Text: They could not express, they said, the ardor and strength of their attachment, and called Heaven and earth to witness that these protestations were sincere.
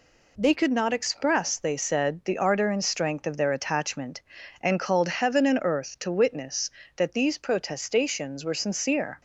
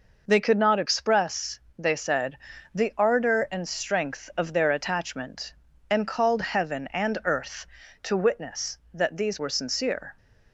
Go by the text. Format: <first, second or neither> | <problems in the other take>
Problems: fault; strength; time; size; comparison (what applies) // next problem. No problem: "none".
first | skips "protestations"; at 9.3 s